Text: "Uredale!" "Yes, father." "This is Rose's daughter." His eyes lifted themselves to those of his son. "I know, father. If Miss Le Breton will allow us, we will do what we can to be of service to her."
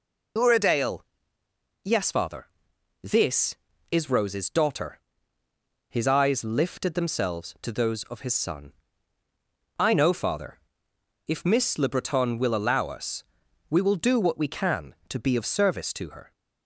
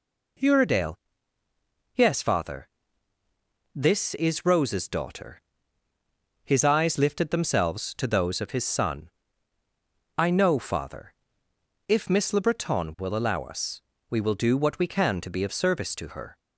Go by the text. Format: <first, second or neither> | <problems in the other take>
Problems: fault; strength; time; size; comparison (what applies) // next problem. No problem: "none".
second | loses the start of "Uredale"; at 0.3 s; 65 ms